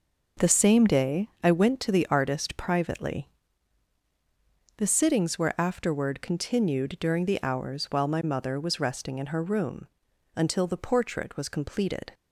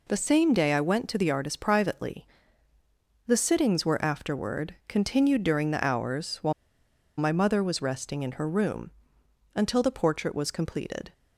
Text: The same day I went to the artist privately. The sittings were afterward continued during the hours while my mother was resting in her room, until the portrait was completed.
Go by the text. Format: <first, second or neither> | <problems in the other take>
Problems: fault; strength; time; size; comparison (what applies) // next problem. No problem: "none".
first | pauses between "while" and "my"; noticeable; at 6.5 s; 0.65 s long